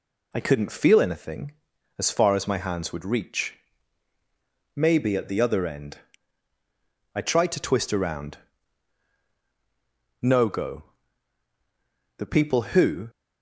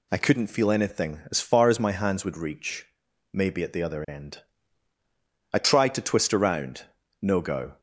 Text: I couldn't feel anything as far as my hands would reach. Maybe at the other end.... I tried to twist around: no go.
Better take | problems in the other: second | goes on to say "The people who"; noticeable; from 12.1 s on; 0.90 s long

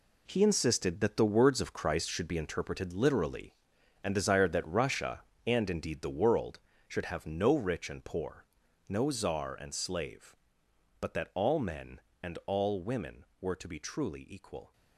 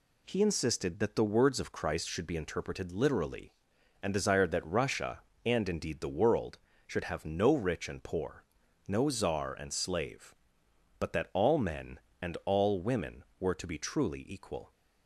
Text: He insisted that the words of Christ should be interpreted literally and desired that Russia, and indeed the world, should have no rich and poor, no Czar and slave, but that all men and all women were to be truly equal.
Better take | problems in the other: second | gets quieter; strong; throughout; 10.5 dB

